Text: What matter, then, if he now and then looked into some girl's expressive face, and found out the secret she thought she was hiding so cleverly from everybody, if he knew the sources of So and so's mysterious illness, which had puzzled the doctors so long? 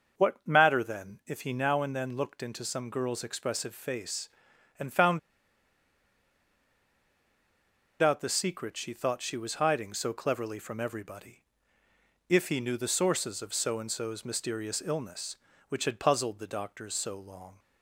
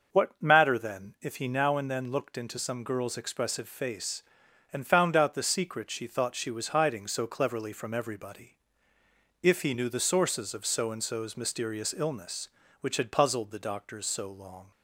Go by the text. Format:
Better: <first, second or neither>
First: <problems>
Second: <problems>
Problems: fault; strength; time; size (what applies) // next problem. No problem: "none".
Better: second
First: starts louder than the rest; until 1.3 s; 6 dB // pauses between "found" and "out"; strong; at 5.1 s; 2.8 s long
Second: starts louder than the rest; until 1.3 s; 6 dB